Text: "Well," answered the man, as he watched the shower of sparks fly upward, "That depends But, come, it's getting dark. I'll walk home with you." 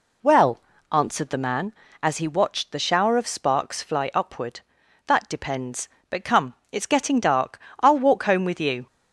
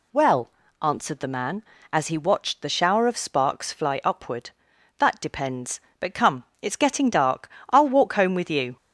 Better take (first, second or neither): second